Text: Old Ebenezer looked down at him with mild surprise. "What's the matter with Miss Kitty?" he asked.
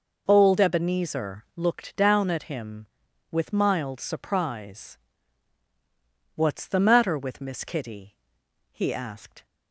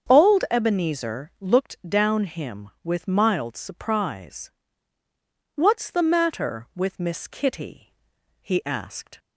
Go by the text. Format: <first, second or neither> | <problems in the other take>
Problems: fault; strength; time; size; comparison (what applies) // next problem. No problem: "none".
first | starts louder than the rest; until 1.1 s; 7 dB // skips "at"; at 2.2 s